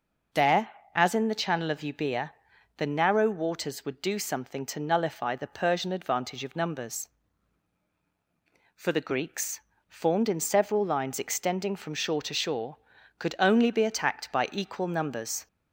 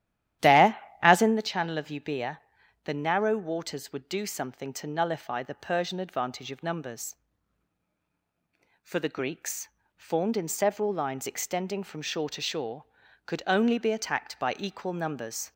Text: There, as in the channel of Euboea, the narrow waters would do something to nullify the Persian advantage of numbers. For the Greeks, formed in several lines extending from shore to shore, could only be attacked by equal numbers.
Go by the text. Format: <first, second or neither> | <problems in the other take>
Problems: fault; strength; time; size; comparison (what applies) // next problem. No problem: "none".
first | starts louder than the rest; strong; until 1.5 s; 12 dB